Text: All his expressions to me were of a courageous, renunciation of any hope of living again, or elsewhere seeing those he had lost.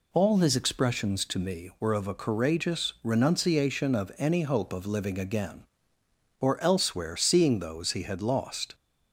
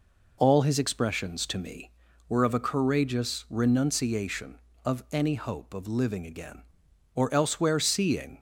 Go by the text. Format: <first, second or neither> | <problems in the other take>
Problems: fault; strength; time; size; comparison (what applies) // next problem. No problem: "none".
first | stops before "those he had lost"; at 8.3 s